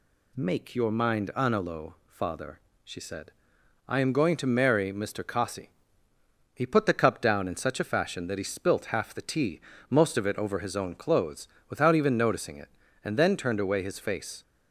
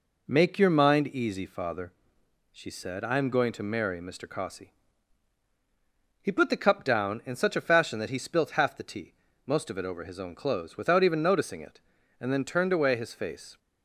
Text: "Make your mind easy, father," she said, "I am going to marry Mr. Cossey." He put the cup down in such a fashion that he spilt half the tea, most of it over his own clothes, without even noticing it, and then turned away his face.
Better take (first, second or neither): second